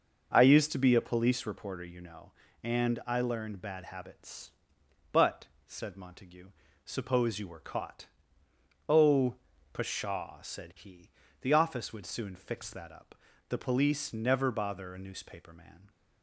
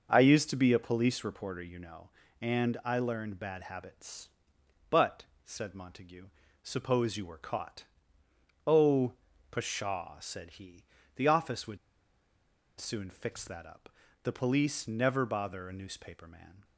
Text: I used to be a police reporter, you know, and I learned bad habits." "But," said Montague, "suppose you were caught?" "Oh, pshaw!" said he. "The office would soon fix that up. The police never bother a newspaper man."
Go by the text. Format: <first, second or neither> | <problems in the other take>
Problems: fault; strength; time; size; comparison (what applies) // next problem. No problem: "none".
first | starts louder than the rest; noticeable; until 1.1 s; 6 dB; noticeable in the first // pauses between "would" and "soon"; at 11.7 s; 1.0 s long